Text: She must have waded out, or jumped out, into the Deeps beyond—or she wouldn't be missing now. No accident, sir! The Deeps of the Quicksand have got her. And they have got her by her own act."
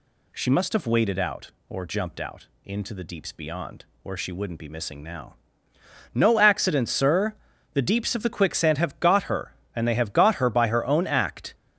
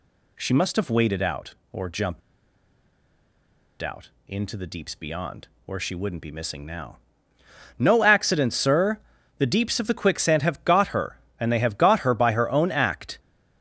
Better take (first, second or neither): first